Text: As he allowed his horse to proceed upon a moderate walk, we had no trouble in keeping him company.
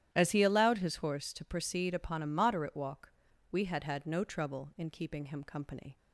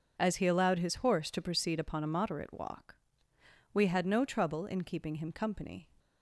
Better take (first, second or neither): second